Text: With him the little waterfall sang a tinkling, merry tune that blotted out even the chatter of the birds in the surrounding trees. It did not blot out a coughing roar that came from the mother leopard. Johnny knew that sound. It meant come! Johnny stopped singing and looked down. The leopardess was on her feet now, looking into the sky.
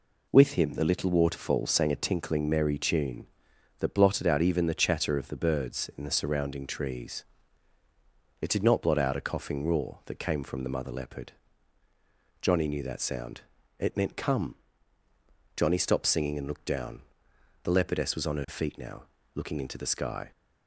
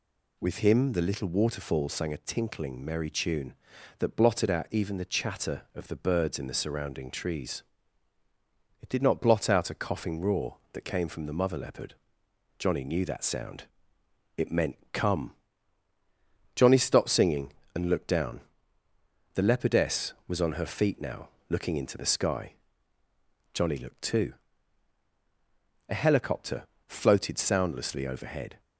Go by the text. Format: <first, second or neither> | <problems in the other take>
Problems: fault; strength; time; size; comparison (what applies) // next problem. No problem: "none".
first | goes on to say "Johnny looked too A helicopter floated soundlessly overhead"; strong; from 23.5 s on; 5.0 s long